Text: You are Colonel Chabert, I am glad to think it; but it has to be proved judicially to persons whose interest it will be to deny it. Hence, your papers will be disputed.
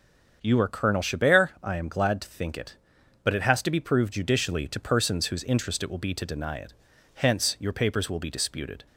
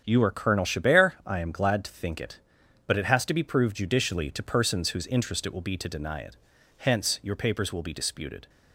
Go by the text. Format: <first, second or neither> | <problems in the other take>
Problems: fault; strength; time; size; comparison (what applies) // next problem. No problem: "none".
first | gets quieter; strong; throughout; 8 dB // starts louder than the rest; strong; until 1.0 s; 8.5 dB; strong in the first